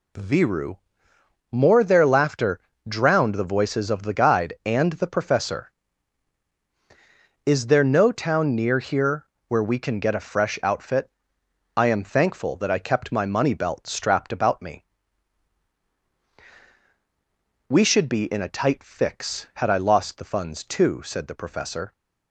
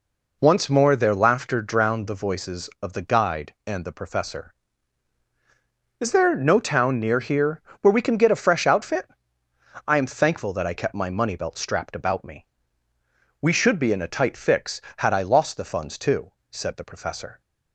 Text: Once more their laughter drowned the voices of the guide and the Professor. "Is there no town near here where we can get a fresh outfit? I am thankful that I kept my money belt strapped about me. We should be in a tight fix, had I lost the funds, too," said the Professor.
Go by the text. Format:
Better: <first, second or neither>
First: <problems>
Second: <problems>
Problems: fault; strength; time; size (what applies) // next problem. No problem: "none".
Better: second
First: says "Viru" for "Once"; at 0.1 s // pauses between "laughter" and "drowned"; slight; at 2.5 s; 0.30 s long // pauses between "here" and "where"; slight; at 9.2 s; 0.20 s long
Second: pauses between "here" and "where"; slight; at 7.6 s; 0.20 s long